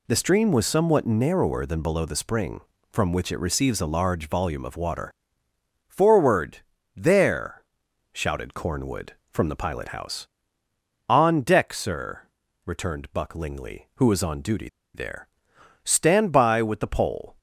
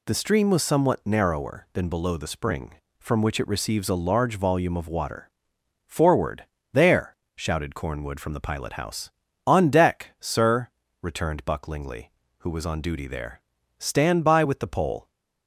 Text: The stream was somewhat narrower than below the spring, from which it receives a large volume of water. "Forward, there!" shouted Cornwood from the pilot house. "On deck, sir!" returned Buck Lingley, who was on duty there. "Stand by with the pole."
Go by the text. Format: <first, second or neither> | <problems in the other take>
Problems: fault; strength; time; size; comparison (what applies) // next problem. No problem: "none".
second | pauses between "duty" and "there"; slight; at 14.6 s; 0.27 s long